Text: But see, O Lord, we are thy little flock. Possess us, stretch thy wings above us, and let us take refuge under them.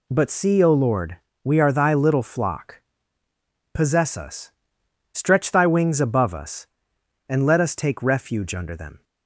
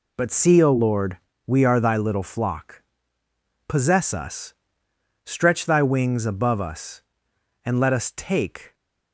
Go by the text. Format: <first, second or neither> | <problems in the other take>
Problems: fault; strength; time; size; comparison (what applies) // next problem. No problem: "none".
first | stops before "refuge under them"; at 8.7 s